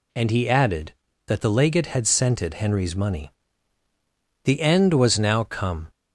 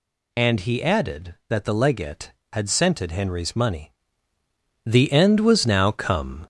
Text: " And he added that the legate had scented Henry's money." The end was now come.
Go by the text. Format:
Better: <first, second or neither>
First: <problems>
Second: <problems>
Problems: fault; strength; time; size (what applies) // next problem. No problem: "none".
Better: first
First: none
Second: gets louder; noticeable; throughout; 4.5 dB